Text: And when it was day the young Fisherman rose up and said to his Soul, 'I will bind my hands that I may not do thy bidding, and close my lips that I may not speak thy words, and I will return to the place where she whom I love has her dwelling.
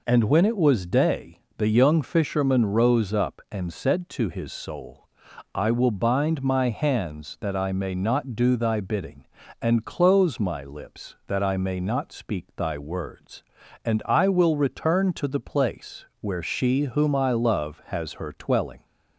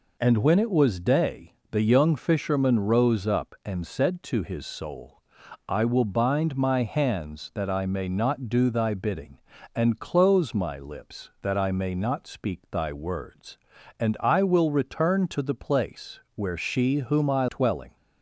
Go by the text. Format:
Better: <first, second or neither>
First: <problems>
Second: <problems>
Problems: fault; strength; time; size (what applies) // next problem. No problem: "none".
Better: first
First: pauses between "day" and "the"; slight; at 1.3 s; 0.18 s long // pauses between "place" and "where"; slight; at 16.0 s; 0.16 s long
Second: pauses between "day" and "the"; slight; at 1.5 s; 0.18 s long // pauses between "place" and "where"; slight; at 16.1 s; 0.16 s long // skips "love has her"; at 17.4 s